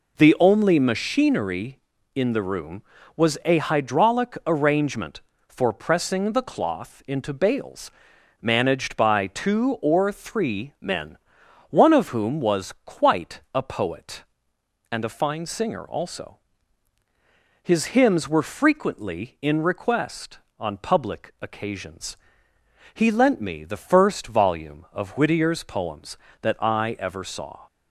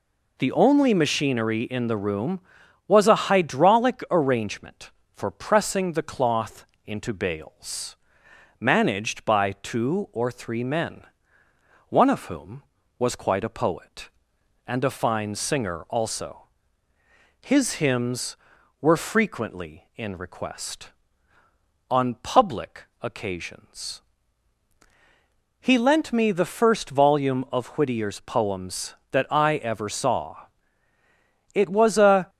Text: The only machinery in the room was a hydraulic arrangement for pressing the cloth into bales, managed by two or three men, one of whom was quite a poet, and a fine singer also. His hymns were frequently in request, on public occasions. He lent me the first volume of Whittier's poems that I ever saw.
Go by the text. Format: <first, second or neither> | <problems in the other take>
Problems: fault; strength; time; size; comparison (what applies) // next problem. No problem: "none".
first | pauses between "cloth" and "into"; slight; at 6.6 s; 0.20 s long // pauses between "public" and "occasions"; slight; at 22.8 s; 0.18 s long // goes on to say "It was a"; noticeable; from 31.5 s on; 0.76 s long